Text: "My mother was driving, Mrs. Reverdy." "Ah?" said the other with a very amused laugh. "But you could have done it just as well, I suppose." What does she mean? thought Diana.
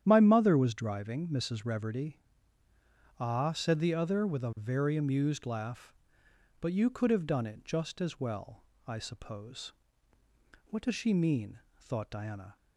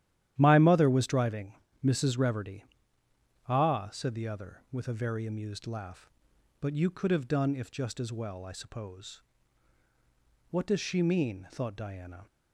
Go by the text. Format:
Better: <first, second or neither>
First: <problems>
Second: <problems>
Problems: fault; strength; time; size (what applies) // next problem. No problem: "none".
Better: first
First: starts louder than the rest; strong; until 1.0 s; 10 dB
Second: starts louder than the rest; strong; until 1.3 s; 11.5 dB // says "if" for "it"; at 7.5 s